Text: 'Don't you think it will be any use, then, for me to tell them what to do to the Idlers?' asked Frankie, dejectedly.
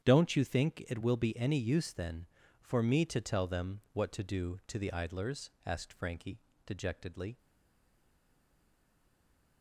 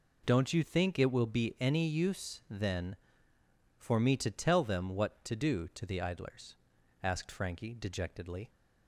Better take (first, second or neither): second